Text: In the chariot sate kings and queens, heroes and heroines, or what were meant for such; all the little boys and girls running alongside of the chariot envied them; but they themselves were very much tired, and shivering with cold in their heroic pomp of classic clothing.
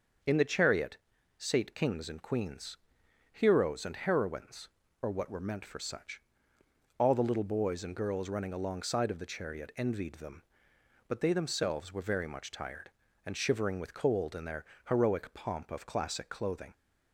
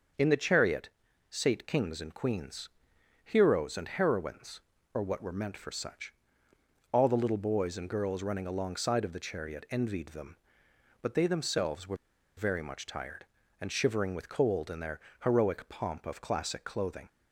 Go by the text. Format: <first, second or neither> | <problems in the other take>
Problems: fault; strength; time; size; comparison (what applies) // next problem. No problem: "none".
first | starts louder than the rest; until 1.5 s; 6.5 dB; also in the first // pauses between "chariot" and "sate"; at 0.8 s; 0.42 s long; also in the first // pauses between "were" and "very"; at 11.9 s; 0.41 s long // pauses between "their" and "heroic"; slight; at 14.9 s; 0.24 s long; slight in the first